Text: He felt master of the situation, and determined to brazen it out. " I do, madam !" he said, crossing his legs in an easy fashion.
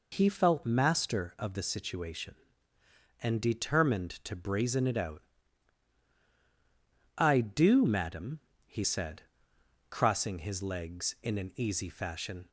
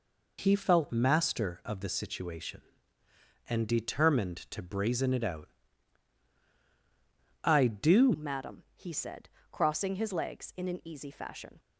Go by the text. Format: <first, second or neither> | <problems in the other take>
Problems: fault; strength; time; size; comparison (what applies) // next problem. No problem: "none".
first | changes voice at "madam"; from 8.1 s on; 3.4 s long